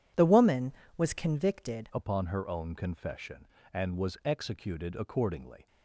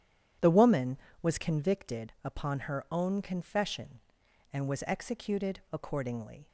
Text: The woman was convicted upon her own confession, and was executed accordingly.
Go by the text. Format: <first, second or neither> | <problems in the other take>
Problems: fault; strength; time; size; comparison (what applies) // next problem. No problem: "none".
second | changes voice at "upon"; from 1.9 s on; 3.7 s long